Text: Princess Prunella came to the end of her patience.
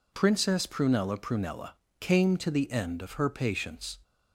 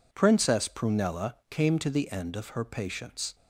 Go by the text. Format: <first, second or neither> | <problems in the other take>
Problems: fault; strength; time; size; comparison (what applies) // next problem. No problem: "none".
second | says "Prunella" twice; at 1.1 s